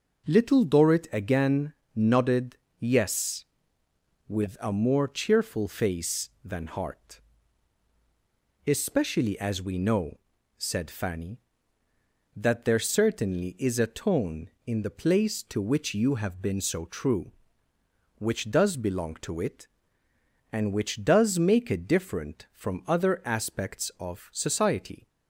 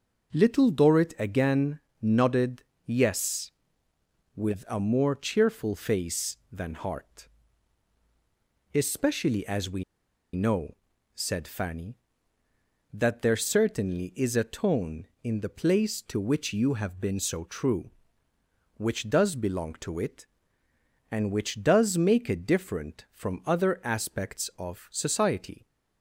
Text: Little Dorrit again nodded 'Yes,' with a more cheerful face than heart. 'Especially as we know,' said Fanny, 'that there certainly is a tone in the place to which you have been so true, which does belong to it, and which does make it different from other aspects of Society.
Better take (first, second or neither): first